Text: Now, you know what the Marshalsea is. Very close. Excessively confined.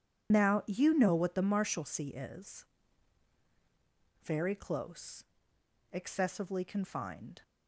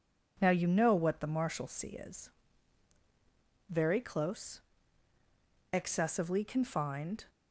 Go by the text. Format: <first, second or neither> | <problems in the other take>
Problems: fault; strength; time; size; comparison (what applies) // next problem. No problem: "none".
second | loses the start of "Now"; at 0.3 s; 65 ms